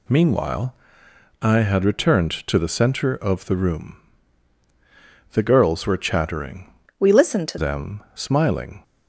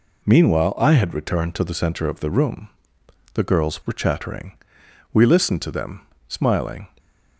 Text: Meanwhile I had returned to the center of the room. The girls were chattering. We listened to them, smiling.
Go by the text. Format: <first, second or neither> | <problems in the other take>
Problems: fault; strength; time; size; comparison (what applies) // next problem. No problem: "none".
second | pauses between "Meanwhile" and "I"; noticeable; at 0.7 s; 0.66 s long // changes voice from "We" to "to"; from 6.9 to 7.5 s; 0.6 s long